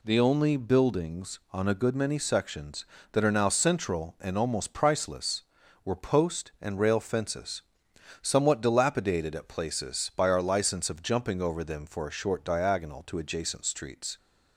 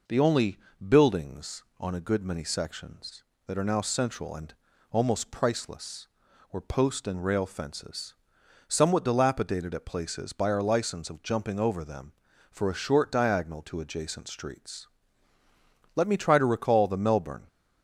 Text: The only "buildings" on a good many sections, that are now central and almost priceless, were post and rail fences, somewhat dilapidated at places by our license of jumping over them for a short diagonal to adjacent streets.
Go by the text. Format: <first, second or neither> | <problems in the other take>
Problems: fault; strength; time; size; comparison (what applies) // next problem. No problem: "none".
first | pauses between "only" and "buildings"; slight; at 0.5 s; 0.30 s long // pauses between "and" and "almost"; at 4.5 s; 0.38 s long // goes on to say "Let me try to recall the Melbourne"; from 15.9 s on; 1.5 s long